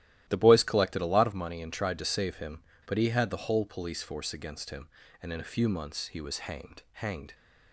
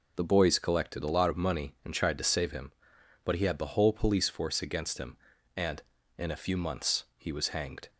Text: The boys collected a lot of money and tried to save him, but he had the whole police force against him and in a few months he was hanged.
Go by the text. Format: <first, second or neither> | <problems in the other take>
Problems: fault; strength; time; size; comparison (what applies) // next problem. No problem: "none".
second | starts louder than the rest; strong; until 1.2 s; 13 dB // says "hanged" twice; at 6.9 s